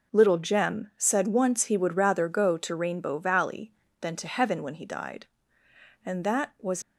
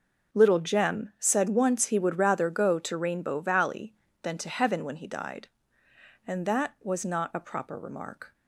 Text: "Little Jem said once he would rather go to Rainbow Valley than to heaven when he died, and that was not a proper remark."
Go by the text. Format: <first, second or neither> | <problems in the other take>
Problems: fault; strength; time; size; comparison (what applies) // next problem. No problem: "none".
second | stops before "not a proper remark"; at 6.8 s